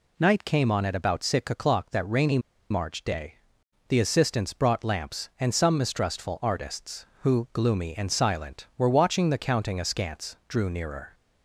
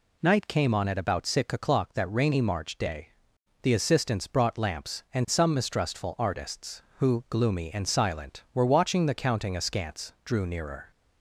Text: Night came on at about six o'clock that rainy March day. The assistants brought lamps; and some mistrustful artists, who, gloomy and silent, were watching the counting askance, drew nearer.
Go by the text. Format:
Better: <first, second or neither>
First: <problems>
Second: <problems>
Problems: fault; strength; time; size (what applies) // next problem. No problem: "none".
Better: second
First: pauses between "rainy" and "March"; slight; at 2.3 s; 0.31 s long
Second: none